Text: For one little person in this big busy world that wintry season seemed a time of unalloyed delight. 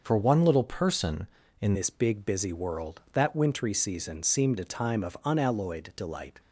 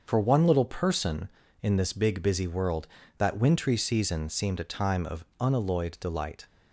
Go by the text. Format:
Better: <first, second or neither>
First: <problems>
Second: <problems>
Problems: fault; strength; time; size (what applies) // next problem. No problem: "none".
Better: second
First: starts louder than the rest; until 1.0 s; 6 dB // changes voice at "this"; from 1.7 s on; 4.6 s long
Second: starts louder than the rest; until 1.0 s; 6.5 dB